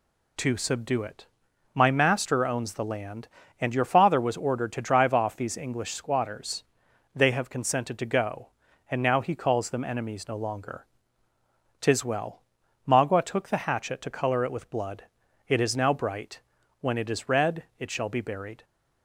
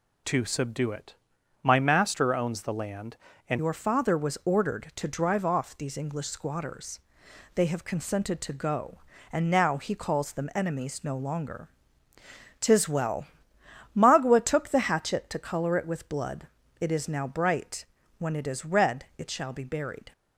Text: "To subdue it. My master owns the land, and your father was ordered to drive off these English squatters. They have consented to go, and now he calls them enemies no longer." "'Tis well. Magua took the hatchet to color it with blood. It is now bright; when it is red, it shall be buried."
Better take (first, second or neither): first